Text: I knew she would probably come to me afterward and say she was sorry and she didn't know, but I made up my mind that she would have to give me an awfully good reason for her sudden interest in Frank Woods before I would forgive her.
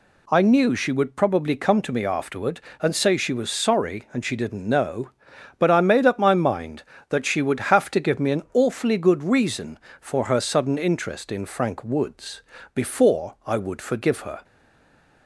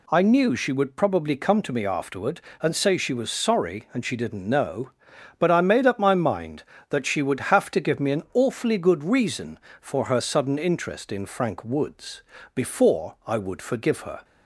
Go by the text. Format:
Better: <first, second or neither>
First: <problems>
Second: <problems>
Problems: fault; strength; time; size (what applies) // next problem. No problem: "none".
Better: second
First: pauses between "Woods" and "before"; slight; at 12.4 s; 0.32 s long // stays silent after the last word; slight; from 14.4 s on; 0.8 s long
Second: pauses between "Woods" and "before"; slight; at 12.2 s; 0.32 s long